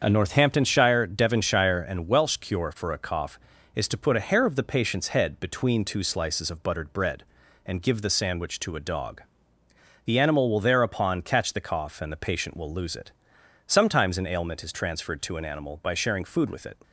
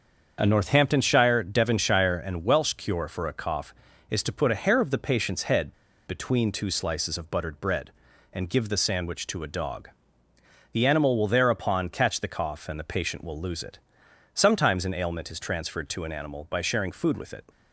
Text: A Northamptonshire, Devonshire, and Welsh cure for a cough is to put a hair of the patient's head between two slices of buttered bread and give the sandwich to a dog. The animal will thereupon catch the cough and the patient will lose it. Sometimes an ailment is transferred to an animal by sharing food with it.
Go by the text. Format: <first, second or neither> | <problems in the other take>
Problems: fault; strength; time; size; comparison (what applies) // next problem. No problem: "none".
first | starts louder than the rest; until 1.4 s; 7 dB; also in the first // pauses between "head" and "between"; slight; at 5.7 s; 0.33 s long